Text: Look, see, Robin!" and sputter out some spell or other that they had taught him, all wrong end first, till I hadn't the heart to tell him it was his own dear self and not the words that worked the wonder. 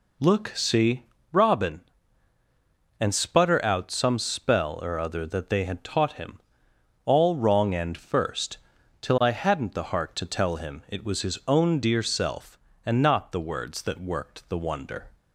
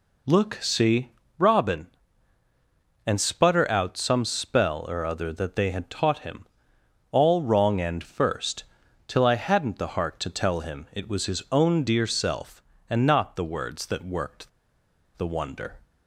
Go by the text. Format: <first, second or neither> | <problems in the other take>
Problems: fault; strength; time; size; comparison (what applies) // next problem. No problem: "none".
first | pauses between "worked" and "the"; noticeable; at 14.4 s; 0.67 s long